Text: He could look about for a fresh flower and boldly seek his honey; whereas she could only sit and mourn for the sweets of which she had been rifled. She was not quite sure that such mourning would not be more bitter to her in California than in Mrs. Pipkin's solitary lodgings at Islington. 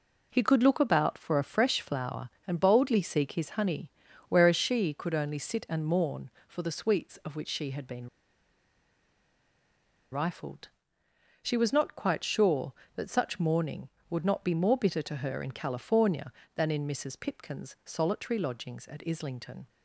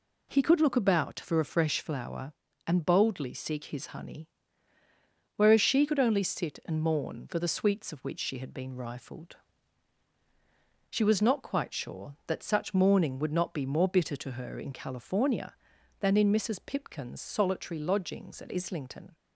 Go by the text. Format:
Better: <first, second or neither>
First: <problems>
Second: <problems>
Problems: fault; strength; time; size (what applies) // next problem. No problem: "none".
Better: second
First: pauses between "been" and "rifled"; strong; at 8.0 s; 2.0 s long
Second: none